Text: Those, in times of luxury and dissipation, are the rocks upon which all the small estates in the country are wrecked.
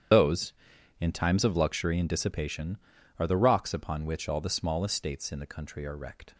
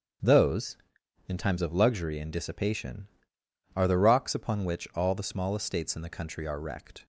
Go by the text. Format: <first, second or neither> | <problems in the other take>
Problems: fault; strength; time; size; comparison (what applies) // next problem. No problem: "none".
second | loses the start of "Those"; at 0.1 s; 70 ms // starts louder than the rest; strong; until 1.6 s; 9 dB; strong in the second